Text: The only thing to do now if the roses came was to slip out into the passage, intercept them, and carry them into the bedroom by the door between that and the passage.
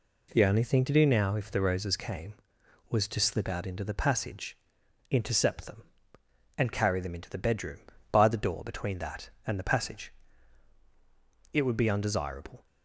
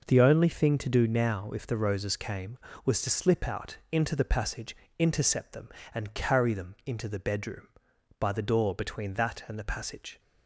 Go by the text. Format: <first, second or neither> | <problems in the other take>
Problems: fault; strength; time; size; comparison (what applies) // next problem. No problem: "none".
second | goes on to say "It would be undesirable"; noticeable; from 11.5 s on; 1.1 s long